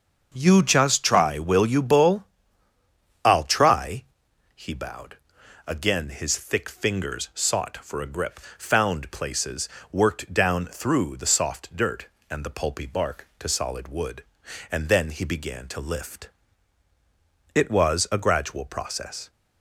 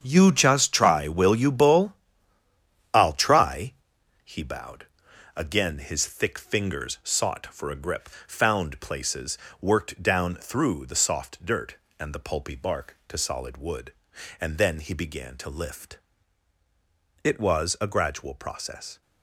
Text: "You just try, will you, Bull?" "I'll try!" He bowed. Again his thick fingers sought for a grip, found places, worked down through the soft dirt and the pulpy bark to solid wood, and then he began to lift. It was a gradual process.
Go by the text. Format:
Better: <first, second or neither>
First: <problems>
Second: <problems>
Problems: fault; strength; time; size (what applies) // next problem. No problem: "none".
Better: first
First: starts louder than the rest; until 1.3 s; 6.5 dB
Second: gets quieter; strong; throughout; 11 dB // starts louder than the rest; strong; until 1.0 s; 8 dB